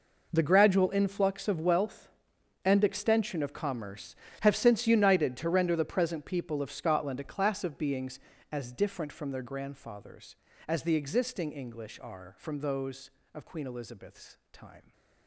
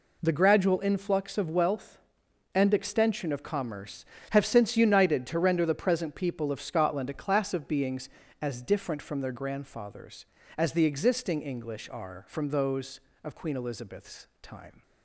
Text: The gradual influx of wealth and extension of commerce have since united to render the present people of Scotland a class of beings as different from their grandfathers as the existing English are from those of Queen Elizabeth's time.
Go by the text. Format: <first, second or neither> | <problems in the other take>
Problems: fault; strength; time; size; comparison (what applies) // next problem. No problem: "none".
second | gets quieter; strong; throughout; 15.5 dB